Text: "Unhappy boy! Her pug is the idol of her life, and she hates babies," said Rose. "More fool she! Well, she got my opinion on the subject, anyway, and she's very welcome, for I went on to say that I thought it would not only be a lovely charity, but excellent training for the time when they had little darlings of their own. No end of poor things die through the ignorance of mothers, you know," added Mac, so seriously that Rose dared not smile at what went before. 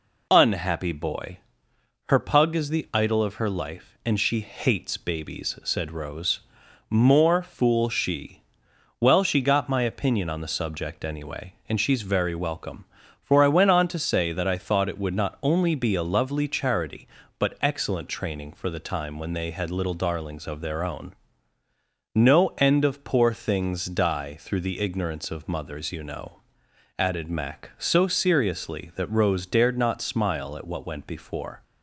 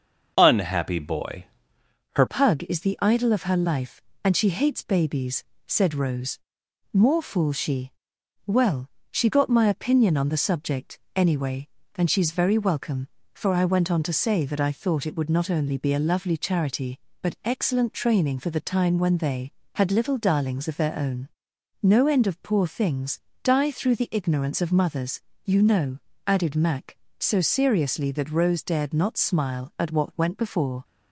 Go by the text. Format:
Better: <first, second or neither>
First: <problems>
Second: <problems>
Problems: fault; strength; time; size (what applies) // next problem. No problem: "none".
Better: first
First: none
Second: starts louder than the rest; until 1.3 s; 6 dB // changes voice at "pug"; from 2.2 s on; 28.6 s long // pauses between "things" and "die"; slight; at 23.2 s; 0.24 s long